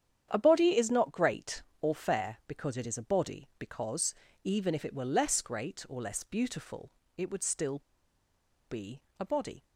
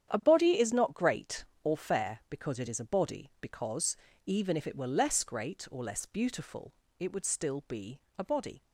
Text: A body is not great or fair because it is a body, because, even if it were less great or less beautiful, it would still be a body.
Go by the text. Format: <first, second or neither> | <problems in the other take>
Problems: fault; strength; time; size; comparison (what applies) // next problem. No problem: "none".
second | starts louder than the rest; strong; until 1.3 s; 9 dB; strong in the second // pauses between "still" and "be"; noticeable; at 7.8 s; 0.89 s long // pauses between "be" and "a"; slight; at 9.0 s; 0.16 s long; slight in the second